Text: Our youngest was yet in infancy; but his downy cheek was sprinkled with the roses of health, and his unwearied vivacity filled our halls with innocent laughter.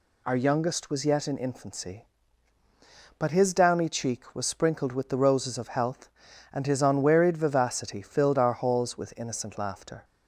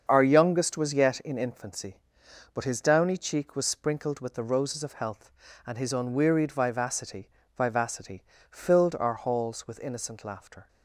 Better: first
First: none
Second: starts louder than the rest; until 1.0 s; 7 dB // says "vivacity" twice; at 7.5 s

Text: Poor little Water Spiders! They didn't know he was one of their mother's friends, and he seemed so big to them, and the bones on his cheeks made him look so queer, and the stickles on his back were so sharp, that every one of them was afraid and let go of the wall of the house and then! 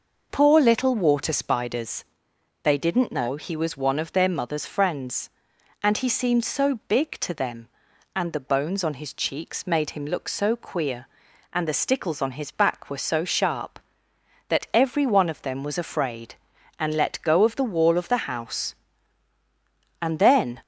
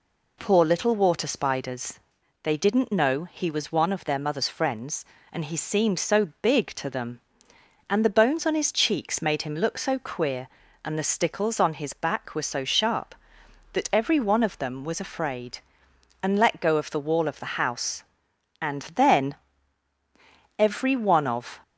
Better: first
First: none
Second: goes on to say "Every one of"; noticeable; from 20.5 s on; 1.0 s long

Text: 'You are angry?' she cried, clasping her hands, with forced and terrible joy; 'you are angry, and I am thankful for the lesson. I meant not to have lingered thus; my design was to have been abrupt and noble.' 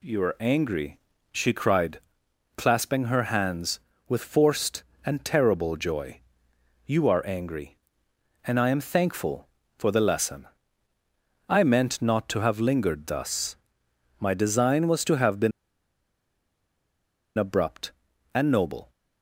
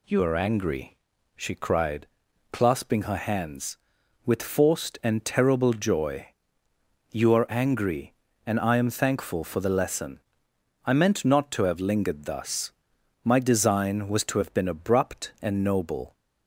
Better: second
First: pauses between "been" and "abrupt"; strong; at 15.5 s; 1.8 s long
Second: none

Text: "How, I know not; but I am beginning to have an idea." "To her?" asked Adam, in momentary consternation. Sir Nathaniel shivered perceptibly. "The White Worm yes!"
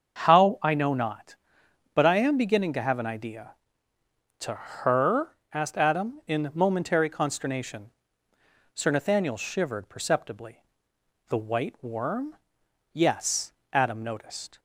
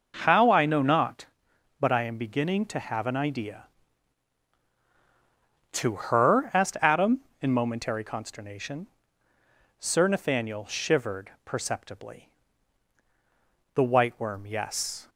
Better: second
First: starts louder than the rest; until 1.2 s; 6.5 dB // pauses between "Worm" and "yes"; noticeable; at 12.3 s; 0.58 s long // goes on to say "Adam noticed"; noticeable; from 13.7 s on; 0.88 s long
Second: none

